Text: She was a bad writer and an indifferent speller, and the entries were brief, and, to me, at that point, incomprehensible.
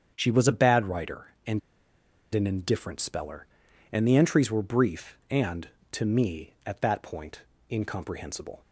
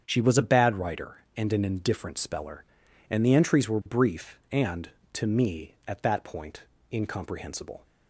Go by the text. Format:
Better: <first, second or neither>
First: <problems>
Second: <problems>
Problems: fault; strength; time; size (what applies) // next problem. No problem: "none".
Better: second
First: starts louder than the rest; strong; until 1.1 s; 7.5 dB // pauses between "and" and "an"; noticeable; at 1.5 s; 0.74 s long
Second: starts louder than the rest; strong; until 1.0 s; 7.5 dB